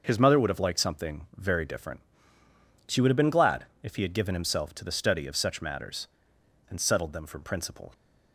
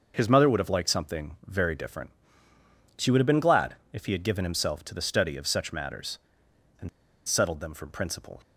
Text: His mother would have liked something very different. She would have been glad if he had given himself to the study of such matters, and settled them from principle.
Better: first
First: pauses between "glad" and "if"; slight; at 3.6 s; 0.16 s long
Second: pauses between "glad" and "if"; slight; at 3.7 s; 0.16 s long // pauses between "and" and "settled"; at 6.8 s; 0.36 s long

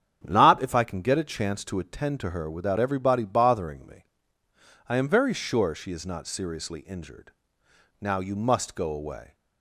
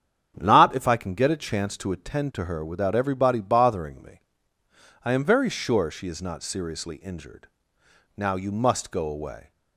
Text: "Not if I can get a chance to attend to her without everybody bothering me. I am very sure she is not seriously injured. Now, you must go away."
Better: neither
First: starts louder than the rest; strong; until 1.2 s; 8 dB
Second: starts louder than the rest; strong; until 1.3 s; 8 dB

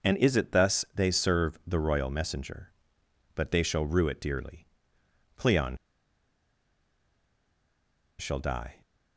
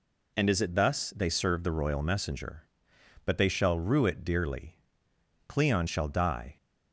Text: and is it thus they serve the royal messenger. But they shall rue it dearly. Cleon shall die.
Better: second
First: pauses between "Cleon" and "shall"; strong; at 5.7 s; 2.4 s long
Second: none

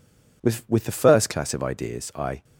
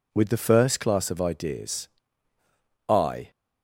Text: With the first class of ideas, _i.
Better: second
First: says "With" twice; at 0.6 s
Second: none

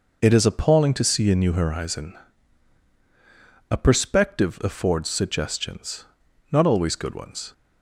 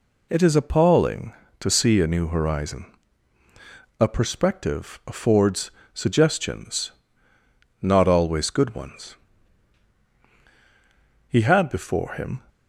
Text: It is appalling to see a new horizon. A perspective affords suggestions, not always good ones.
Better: first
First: none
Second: pauses between "affords" and "suggestions"; slight; at 5.7 s; 0.22 s long // goes on to say "He had before him"; noticeable; from 11.2 s on; 1.1 s long

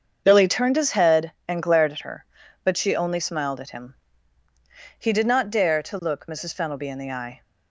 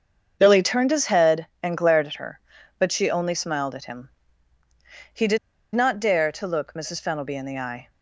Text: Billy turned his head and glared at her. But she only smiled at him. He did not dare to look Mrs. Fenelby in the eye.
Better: first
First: starts louder than the rest; until 1.2 s; 7 dB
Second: starts louder than the rest; until 1.4 s; 7 dB // pauses between "did" and "not"; at 5.3 s; 0.37 s long

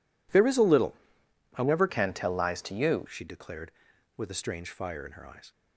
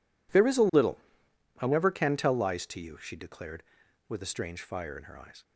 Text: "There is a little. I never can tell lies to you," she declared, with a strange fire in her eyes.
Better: second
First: changes voice from "can" to "you"; from 1.8 to 3.0 s; 1.2 s long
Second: none

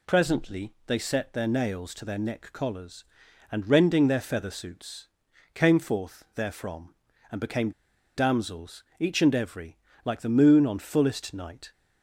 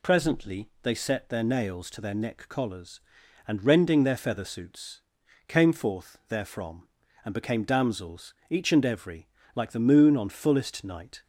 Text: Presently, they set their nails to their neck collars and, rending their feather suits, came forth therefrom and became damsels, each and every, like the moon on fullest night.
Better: second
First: pauses between "became" and "damsels"; at 7.7 s; 0.45 s long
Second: none

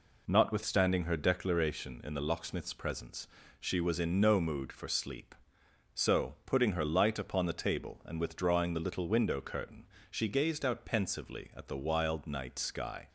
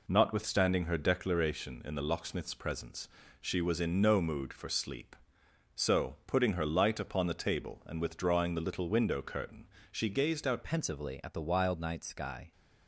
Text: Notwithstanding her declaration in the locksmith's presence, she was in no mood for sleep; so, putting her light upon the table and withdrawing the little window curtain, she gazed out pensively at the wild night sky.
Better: first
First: none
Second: changes voice at "pensively"; from 10.6 s on; 1.9 s long

